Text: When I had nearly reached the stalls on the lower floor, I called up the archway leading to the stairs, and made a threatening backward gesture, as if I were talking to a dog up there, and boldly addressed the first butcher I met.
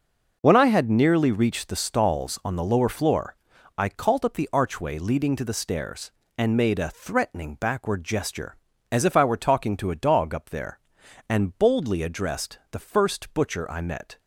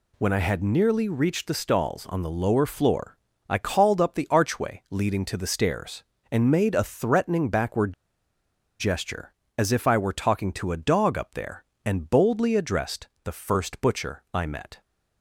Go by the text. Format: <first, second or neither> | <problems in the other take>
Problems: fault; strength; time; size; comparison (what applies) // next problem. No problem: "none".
first | pauses between "backward" and "gesture"; noticeable; at 7.9 s; 0.86 s long // pauses between "addressed" and "the"; slight; at 13.0 s; 0.16 s long